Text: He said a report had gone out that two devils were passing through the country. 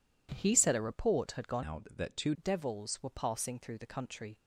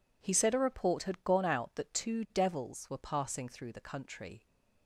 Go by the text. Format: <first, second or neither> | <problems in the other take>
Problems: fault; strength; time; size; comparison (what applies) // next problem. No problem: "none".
second | changes voice from "out" to "two"; from 1.6 to 2.3 s; 0.7 s long